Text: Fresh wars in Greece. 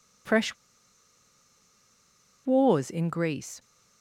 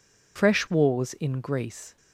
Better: second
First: pauses between "Fresh" and "wars"; strong; at 0.5 s; 1.9 s long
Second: none

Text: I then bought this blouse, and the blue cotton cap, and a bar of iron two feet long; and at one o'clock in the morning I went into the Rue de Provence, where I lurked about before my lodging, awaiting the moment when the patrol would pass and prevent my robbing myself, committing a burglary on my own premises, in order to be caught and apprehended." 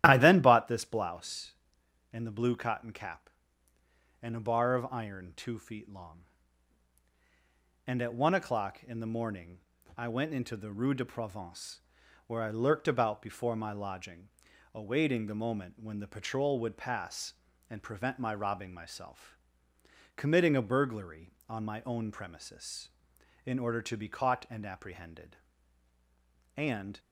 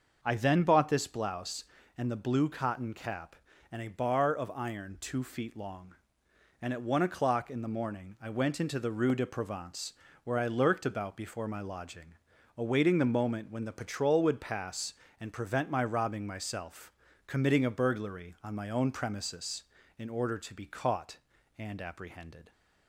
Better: second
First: starts louder than the rest; strong; until 1.0 s; 12.5 dB // pauses between "morning" and "I"; at 9.5 s; 0.40 s long // goes on to say "And"; slight; from 26.5 s on; 0.44 s long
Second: starts louder than the rest; until 1.2 s; 6 dB

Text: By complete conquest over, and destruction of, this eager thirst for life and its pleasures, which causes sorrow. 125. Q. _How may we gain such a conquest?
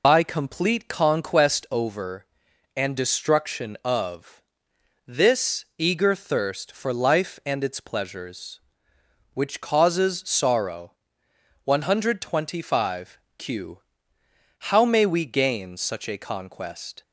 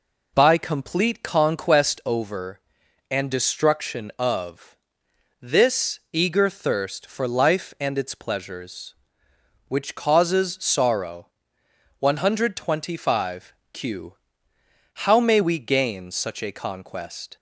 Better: second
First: loses the start of "By"; at 0.0 s; 35 ms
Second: none

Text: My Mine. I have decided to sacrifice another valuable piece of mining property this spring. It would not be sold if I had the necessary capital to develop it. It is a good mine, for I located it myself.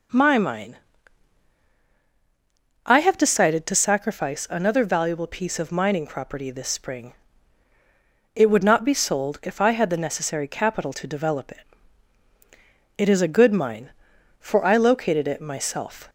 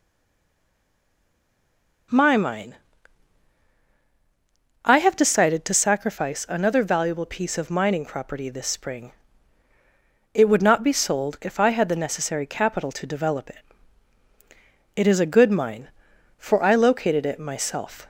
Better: first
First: none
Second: stays silent before the first word; noticeable; until 2.1 s; 2.1 s long

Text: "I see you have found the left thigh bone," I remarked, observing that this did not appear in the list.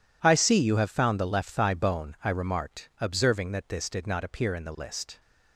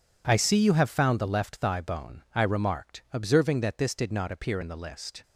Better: second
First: gets quieter; strong; throughout; 15.5 dB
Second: none

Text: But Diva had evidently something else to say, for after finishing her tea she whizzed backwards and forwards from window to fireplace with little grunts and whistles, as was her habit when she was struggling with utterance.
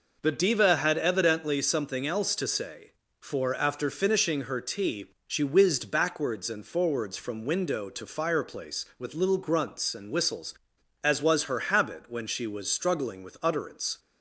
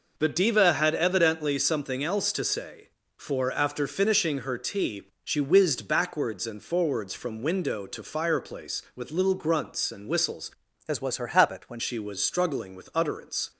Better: first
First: pauses between "tea" and "she"; slight; at 5.1 s; 0.16 s long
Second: pauses between "tea" and "she"; slight; at 5.0 s; 0.16 s long // changes voice from "as" to "when"; from 10.8 to 11.7 s; 0.9 s long

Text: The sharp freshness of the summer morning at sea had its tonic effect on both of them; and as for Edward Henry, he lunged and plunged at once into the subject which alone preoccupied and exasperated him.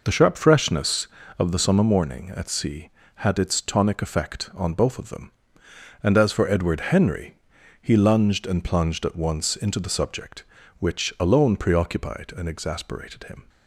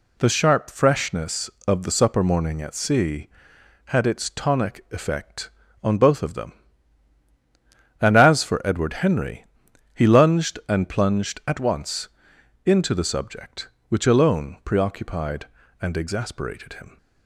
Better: first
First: none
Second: says "supper" for "summer"; at 1.9 s // pauses between "once" and "into"; noticeable; at 12.0 s; 0.56 s long

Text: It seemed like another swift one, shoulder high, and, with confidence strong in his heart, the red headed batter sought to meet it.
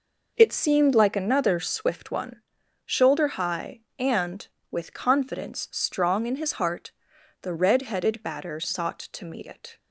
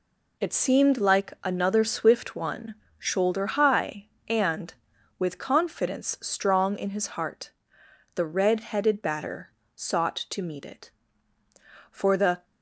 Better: first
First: none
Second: pauses between "batter" and "sought"; slight; at 9.5 s; 0.26 s long // goes on to say "For the"; from 11.9 s on; 0.54 s long

